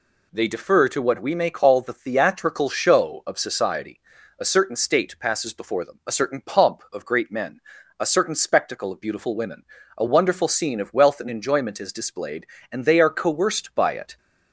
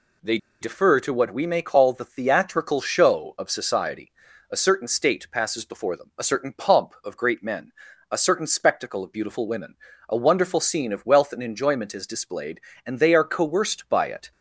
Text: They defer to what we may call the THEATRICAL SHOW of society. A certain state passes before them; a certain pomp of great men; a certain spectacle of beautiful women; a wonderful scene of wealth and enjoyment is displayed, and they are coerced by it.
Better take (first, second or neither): first